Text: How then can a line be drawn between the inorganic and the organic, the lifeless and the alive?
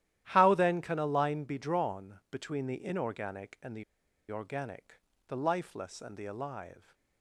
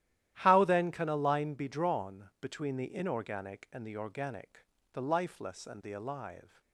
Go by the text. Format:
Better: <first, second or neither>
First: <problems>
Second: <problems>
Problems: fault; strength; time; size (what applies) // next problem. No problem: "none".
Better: second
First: starts louder than the rest; strong; until 1.2 s; 13 dB // pauses between "the" and "organic"; noticeable; at 3.8 s; 0.47 s long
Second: starts louder than the rest; strong; until 1.3 s; 12.5 dB